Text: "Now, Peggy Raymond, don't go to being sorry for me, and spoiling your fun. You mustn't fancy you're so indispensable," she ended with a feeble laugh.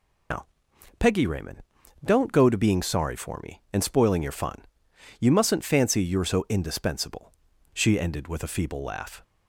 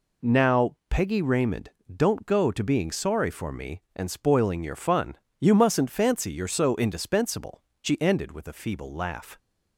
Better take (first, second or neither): second